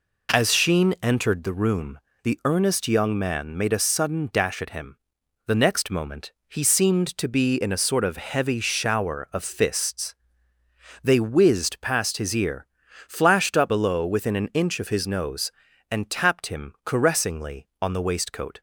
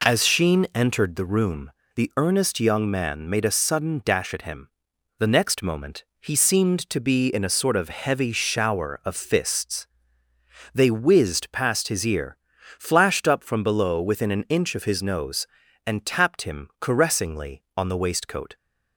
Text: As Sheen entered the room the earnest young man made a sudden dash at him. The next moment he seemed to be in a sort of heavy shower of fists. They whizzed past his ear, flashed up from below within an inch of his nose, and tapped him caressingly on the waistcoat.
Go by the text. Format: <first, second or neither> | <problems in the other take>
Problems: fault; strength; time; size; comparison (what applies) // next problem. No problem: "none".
second | pauses between "room" and "the"; slight; at 1.9 s; 0.24 s long; slight in the second // pauses between "moment" and "he"; slight; at 6.3 s; 0.18 s long; slight in the second // skips "from"; at 13.6 s